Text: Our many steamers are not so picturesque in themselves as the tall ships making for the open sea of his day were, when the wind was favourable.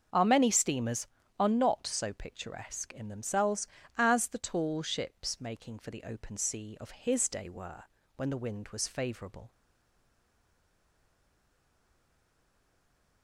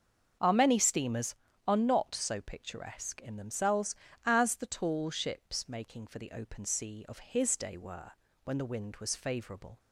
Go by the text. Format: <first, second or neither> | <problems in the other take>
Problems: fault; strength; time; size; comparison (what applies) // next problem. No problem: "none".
second | starts louder than the rest; until 1.4 s; 7 dB; also in the second // stays silent after the last word; strong; from 9.5 s on; 3.7 s long